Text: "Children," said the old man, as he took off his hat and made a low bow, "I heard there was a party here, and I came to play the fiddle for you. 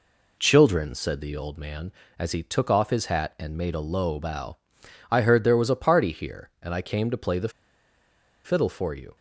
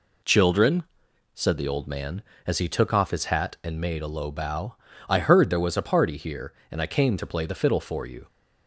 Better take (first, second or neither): second